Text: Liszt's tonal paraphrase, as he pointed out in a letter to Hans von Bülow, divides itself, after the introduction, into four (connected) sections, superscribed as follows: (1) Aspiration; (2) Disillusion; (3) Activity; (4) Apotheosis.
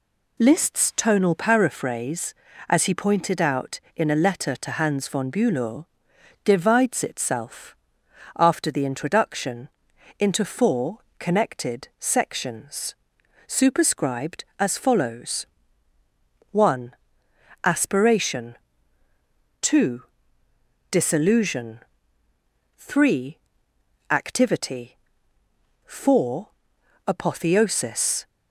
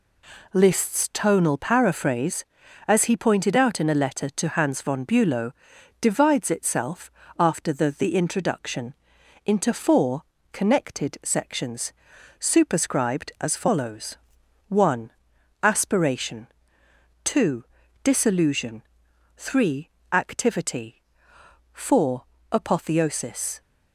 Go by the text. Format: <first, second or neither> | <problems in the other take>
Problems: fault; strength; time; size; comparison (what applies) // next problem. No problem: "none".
first | says "the" twice; at 7.9 s